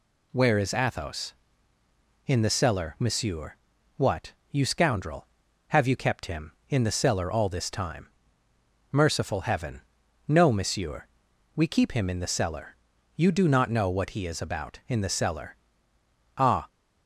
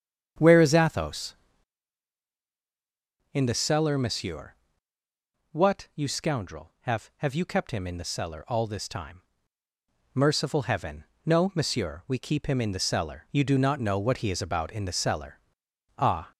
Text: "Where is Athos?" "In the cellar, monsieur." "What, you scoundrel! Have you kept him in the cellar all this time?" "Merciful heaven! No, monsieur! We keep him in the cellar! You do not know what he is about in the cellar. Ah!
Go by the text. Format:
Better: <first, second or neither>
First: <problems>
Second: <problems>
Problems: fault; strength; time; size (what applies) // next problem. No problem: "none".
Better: first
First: none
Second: starts louder than the rest; strong; until 3.4 s; 8.5 dB // says "Have" twice; at 7.1 s